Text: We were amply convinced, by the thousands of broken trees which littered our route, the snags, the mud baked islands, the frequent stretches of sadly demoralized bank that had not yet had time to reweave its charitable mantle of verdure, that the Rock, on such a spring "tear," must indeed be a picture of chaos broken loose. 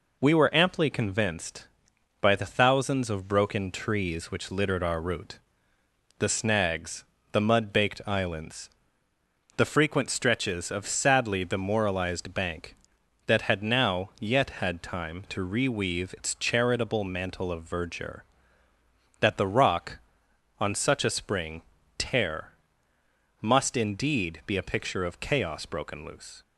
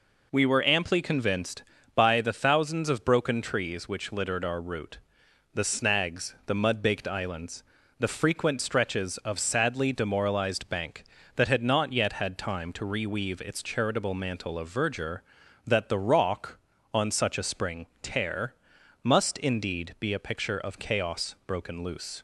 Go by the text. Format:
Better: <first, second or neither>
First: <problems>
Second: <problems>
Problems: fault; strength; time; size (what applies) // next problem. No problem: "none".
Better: second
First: says "now" for "not"; at 13.6 s // pauses between "spring" and "tear"; slight; at 21.6 s; 0.34 s long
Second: pauses between "spring" and "tear"; slight; at 17.8 s; 0.16 s long